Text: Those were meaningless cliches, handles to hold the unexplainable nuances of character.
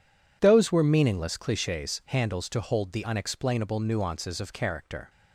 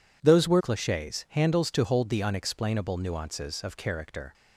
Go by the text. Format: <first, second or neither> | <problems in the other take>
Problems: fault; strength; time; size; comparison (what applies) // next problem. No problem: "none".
first | skips "meaningless"; at 0.5 s